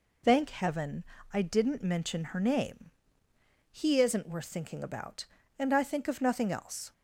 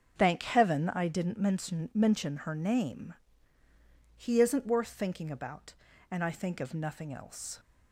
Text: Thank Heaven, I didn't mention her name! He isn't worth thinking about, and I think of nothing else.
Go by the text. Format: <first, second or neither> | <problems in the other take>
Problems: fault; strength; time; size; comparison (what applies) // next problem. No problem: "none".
first | starts louder than the rest; until 1.2 s; 6.5 dB // says "mention" twice; at 1.9 s